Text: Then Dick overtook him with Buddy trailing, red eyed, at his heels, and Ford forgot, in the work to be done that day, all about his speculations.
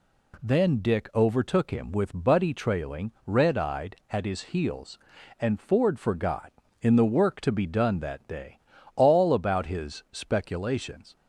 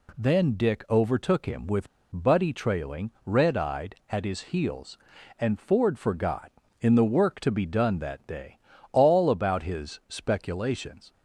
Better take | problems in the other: first | pauses between "with" and "Buddy"; slight; at 1.8 s; 0.26 s long

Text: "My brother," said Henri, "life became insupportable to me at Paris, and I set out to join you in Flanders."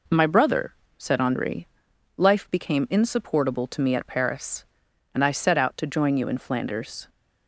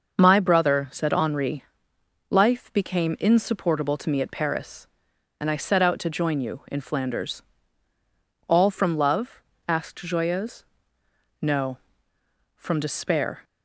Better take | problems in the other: first | starts louder than the rest; until 1.2 s; 6 dB // goes on to say "All from love asked Joyeuse No from despair"; strong; from 8.4 s on; 4.9 s long

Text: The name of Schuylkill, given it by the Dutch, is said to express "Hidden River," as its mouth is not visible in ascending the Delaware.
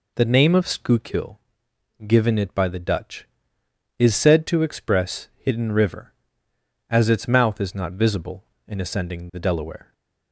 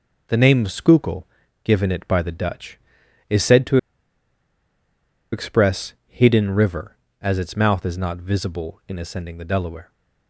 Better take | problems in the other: first | pauses between "to" and "express"; strong; at 3.7 s; 1.5 s long

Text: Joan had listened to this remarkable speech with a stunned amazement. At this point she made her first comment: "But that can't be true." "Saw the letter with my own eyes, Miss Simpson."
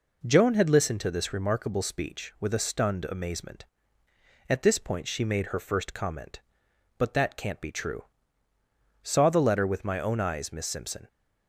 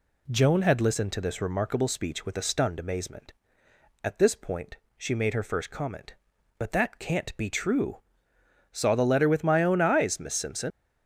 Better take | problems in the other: first | pauses between "point" and "she"; slight; at 4.7 s; 0.22 s long // leaves "Simpson" unfinished; at 10.7 s; 100 ms

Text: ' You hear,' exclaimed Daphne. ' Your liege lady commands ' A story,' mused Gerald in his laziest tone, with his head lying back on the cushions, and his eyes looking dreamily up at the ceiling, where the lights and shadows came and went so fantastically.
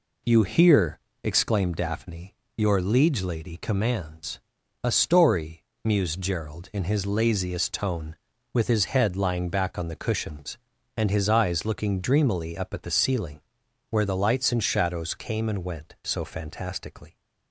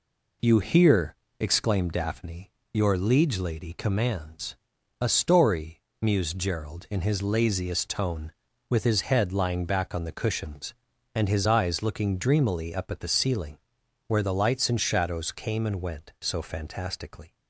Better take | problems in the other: neither | none

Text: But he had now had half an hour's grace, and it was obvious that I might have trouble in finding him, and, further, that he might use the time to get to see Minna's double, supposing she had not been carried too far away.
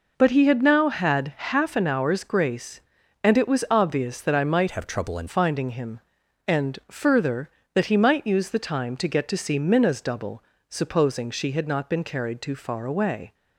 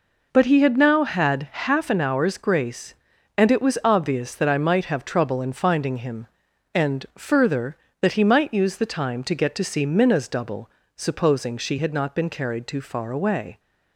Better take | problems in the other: second | changes voice from "have" to "in"; from 4.7 to 5.2 s; 0.5 s long

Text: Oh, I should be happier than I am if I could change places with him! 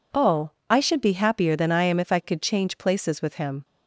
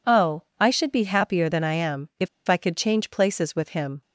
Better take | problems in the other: first | pauses between "if" and "I"; slight; at 2.2 s; 0.20 s long

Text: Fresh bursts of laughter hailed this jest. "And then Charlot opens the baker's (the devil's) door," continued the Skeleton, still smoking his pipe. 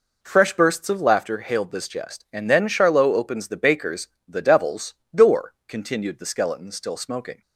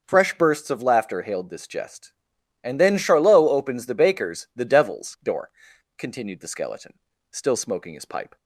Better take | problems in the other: second | stops before "his pipe"; at 7.4 s

